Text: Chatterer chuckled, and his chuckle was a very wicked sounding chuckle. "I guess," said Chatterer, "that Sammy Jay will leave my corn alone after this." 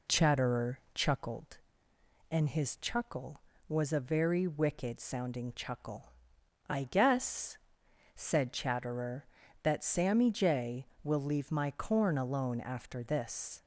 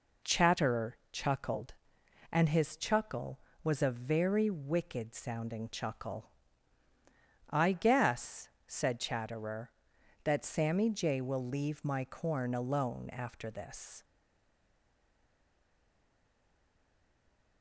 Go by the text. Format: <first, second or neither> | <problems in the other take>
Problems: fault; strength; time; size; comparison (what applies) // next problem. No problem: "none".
first | stays silent after the last word; strong; from 14.0 s on; 3.6 s long